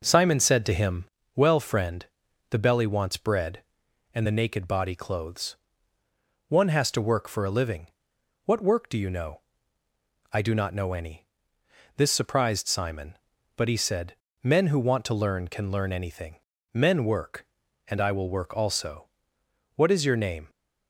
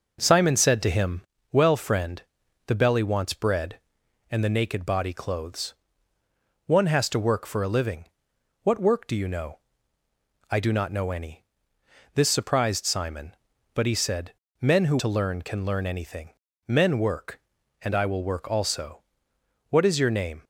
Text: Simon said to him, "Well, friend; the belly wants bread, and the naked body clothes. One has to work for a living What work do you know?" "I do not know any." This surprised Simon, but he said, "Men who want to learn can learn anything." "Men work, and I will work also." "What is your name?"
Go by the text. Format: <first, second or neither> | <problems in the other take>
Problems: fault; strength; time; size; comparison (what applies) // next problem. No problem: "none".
first | pauses between "living" and "What"; noticeable; at 8.0 s; 0.60 s long; noticeable in the first // skips "want"; at 14.9 s